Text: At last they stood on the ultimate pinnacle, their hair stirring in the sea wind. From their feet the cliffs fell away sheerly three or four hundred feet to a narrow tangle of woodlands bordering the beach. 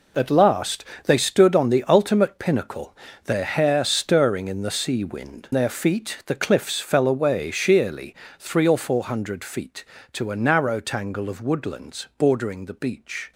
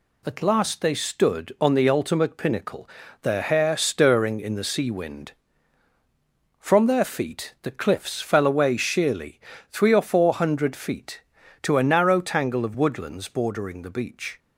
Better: second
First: pauses between "last" and "they"; slight; at 0.8 s; 0.22 s long // skips "From"; at 5.4 s // pauses between "sheerly" and "three"; slight; at 8.1 s; 0.24 s long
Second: pauses between "sheerly" and "three"; slight; at 9.4 s; 0.28 s long

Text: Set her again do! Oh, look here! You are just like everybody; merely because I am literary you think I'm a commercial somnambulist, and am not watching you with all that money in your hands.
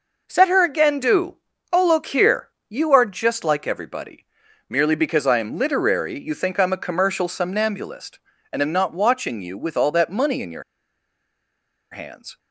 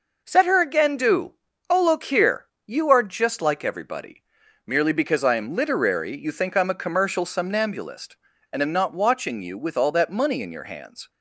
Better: second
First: pauses between "your" and "hands"; strong; at 10.6 s; 1.2 s long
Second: none

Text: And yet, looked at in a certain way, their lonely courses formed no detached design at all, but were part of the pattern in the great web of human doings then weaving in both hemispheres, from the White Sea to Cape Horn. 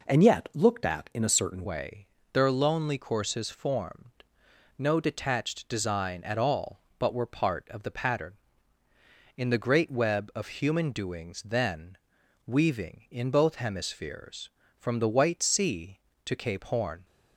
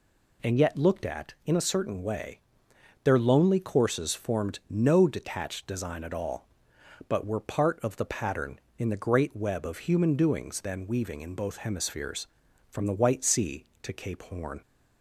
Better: second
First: changes voice at "way"; from 1.6 s on; 15.4 s long // pauses between "formed" and "no"; noticeable; at 4.1 s; 0.68 s long // pauses between "then" and "weaving"; noticeable; at 11.9 s; 0.50 s long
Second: none

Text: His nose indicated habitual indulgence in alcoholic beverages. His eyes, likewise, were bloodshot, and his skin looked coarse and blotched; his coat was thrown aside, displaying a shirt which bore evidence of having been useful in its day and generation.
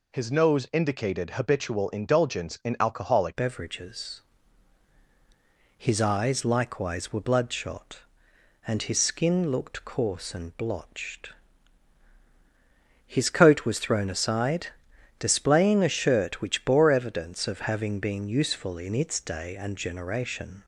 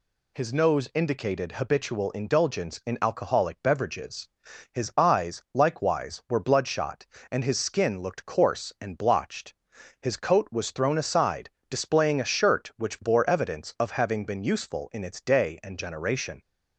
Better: second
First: changes voice at "beverages"; from 3.3 s on; 17.3 s long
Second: none

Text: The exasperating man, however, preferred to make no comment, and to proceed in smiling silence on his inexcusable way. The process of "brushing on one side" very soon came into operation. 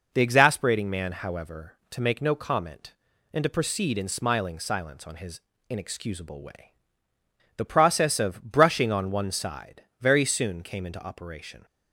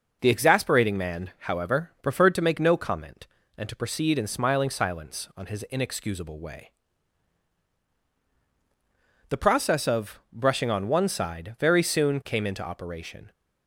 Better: second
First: skips "preferred"; at 1.8 s // pauses between "his" and "inexcusable"; slight; at 5.3 s; 0.30 s long // pauses between "side" and "very"; slight; at 9.8 s; 0.18 s long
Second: none

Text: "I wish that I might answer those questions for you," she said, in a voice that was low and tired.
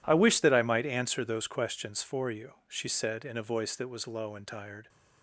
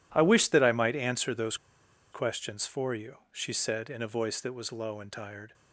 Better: first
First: none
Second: pauses between "those" and "questions"; noticeable; at 1.5 s; 0.56 s long

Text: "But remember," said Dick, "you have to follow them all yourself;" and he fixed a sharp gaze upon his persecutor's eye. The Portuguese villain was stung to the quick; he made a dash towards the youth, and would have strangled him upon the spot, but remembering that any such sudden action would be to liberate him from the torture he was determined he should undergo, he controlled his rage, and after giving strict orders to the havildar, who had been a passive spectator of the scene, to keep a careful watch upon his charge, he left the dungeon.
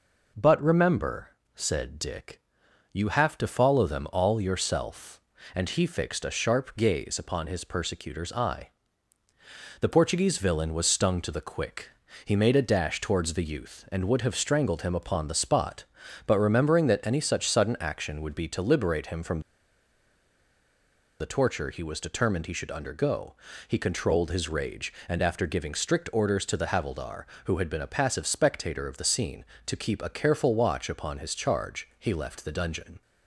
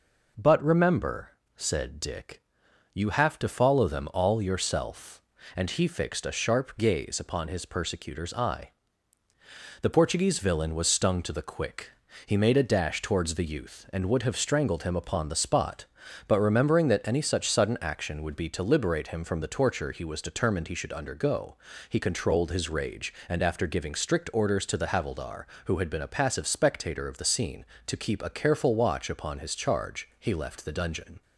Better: second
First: pauses between "from" and "the"; strong; at 19.3 s; 1.8 s long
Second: none

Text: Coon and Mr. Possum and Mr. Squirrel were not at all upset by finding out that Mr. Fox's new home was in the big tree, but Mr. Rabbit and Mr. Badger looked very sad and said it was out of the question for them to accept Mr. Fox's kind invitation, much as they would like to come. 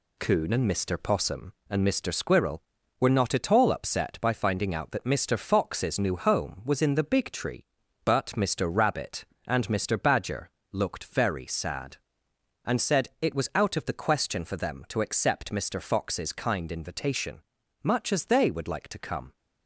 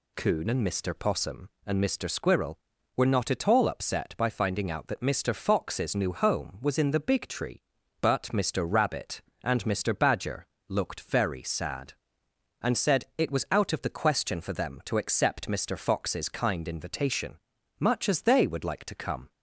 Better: second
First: gets quieter; noticeable; throughout; 5.5 dB // pauses between "Badger" and "looked"; slight; at 10.4 s; 0.22 s long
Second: pauses between "Badger" and "looked"; slight; at 10.4 s; 0.22 s long

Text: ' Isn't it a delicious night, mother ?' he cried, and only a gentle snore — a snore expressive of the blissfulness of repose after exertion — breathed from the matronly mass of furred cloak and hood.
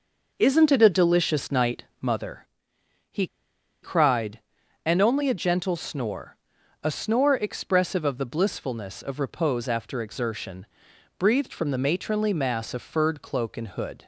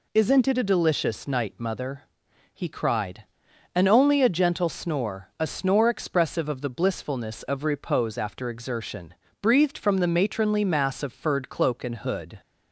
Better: second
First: pauses between "he" and "cried"; noticeable; at 3.2 s; 0.56 s long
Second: none

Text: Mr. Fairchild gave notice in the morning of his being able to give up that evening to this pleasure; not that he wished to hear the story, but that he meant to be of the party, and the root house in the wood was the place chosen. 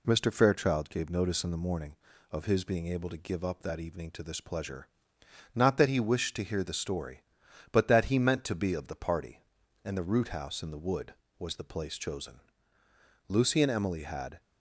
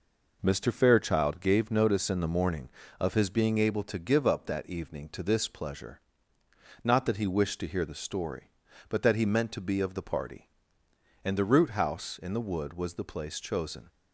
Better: second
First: goes on to say "Lucy and Emily had"; noticeable; from 13.2 s on; 1.1 s long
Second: none

